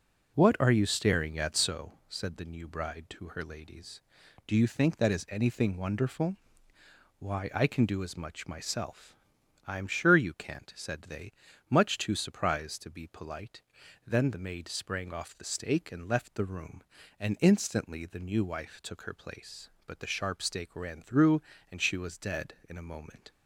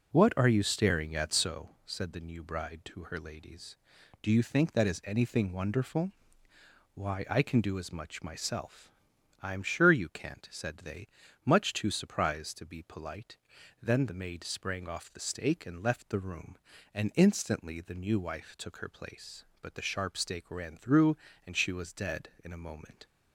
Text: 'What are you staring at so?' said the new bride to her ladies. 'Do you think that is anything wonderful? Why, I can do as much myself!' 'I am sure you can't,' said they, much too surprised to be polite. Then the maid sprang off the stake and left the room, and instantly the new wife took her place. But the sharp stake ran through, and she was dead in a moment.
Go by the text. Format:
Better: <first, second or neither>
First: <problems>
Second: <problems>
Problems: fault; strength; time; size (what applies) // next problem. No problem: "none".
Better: neither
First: none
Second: none